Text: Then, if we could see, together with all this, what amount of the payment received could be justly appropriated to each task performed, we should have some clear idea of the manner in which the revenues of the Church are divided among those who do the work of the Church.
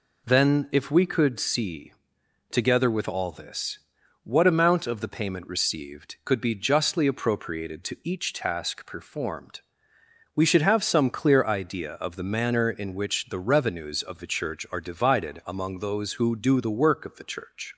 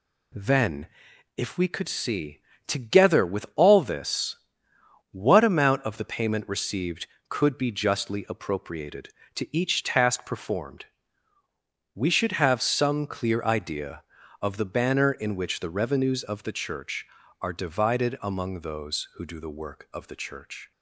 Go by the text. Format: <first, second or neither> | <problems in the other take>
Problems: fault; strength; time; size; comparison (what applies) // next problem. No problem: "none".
first | says "banner" for "manner"; at 14.6 s